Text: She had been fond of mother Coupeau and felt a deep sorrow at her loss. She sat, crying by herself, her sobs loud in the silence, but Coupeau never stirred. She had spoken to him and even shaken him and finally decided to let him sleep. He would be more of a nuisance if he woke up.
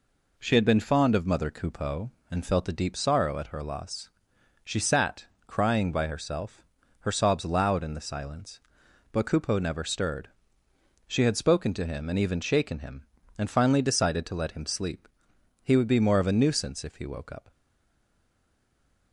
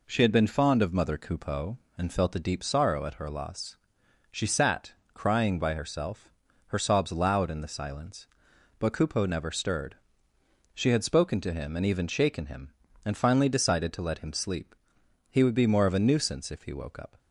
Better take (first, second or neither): second